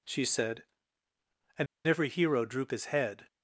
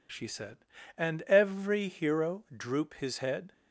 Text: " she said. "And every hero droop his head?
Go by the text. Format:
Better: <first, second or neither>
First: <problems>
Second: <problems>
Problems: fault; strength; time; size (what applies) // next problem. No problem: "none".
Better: second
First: pauses between "And" and "every"; slight; at 1.6 s; 0.18 s long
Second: none